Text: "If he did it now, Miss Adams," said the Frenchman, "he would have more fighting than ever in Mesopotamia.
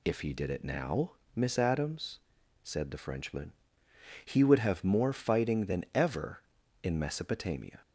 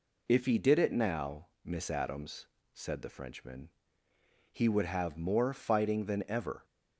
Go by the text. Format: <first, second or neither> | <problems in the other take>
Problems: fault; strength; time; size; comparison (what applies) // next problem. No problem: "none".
first | stops before "in Mesopotamia"; at 6.6 s